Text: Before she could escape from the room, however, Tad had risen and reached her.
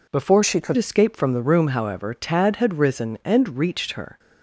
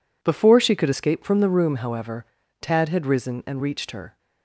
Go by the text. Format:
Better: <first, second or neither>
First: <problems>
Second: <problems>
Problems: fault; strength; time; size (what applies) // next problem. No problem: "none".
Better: second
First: changes voice from "she" to "could"; from 0.4 to 0.7 s; 0.3 s long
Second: none